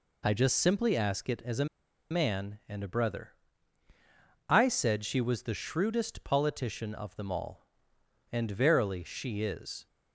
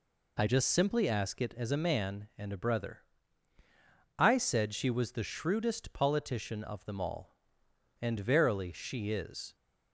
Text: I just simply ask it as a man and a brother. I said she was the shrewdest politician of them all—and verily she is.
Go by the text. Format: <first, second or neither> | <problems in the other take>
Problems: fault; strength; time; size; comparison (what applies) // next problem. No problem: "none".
second | pauses between "a" and "man"; at 1.6 s; 0.44 s long